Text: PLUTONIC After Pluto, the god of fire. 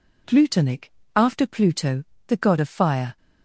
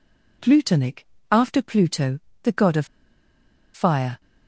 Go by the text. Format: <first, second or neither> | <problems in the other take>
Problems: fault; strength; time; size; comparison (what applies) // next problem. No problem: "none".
first | pauses between "PLUTONIC" and "After"; slight; at 1.0 s; 0.24 s long; slight in the first // pauses between "of" and "fire"; noticeable; at 2.8 s; 0.88 s long